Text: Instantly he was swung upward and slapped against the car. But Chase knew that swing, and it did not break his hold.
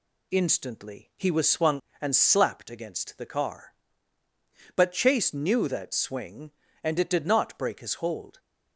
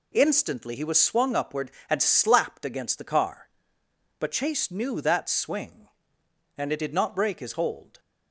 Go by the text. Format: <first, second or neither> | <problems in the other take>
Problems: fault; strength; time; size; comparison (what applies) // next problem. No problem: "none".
second | skips "upward"; at 1.9 s